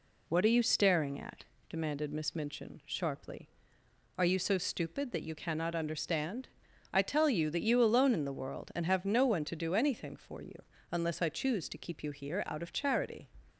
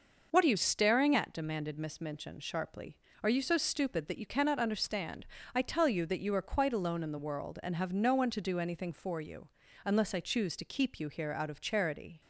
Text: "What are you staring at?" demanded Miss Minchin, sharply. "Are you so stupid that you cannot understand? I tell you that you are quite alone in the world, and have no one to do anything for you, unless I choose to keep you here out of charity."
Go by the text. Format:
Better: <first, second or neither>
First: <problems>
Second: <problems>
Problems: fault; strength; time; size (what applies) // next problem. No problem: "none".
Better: second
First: skips "are quite"; at 7.8 s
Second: none